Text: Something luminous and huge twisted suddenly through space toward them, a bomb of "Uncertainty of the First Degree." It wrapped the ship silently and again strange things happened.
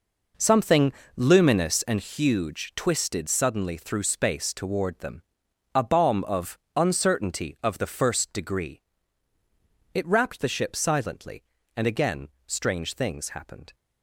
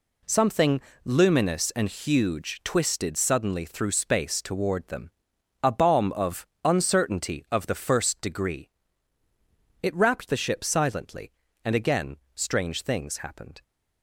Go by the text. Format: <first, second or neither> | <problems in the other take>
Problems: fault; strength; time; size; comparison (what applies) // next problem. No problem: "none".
second | starts louder than the rest; noticeable; until 2.0 s; 5 dB // pauses between "Something" and "luminous"; slight; at 0.9 s; 0.22 s long; slight in the second // pauses between "of" and "Uncertainty"; slight; at 6.5 s; 0.16 s long; slight in the second // pauses between "again" and "strange"; slight; at 12.2 s; 0.18 s long; slight in the second